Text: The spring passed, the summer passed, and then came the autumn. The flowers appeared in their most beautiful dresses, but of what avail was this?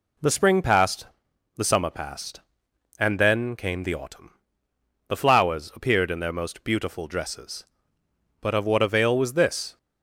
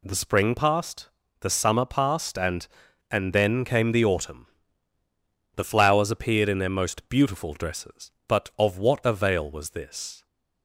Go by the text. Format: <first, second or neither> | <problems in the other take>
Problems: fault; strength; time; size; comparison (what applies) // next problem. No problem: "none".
first | says "and" twice; at 3.0 s